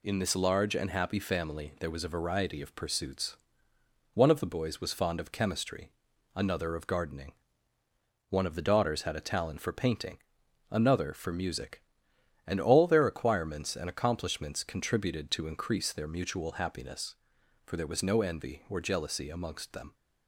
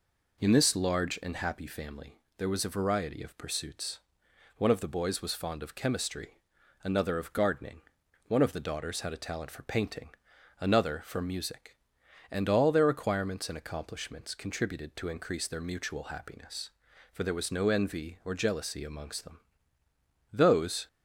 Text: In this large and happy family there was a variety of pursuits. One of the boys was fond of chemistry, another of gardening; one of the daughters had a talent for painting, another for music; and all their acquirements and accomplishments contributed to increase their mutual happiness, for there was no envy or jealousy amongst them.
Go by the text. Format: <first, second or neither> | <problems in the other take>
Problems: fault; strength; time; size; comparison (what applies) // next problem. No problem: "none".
first | pauses between "family" and "there"; slight; at 2.1 s; 0.22 s long // goes on to say "Those"; from 20.3 s on; 0.56 s long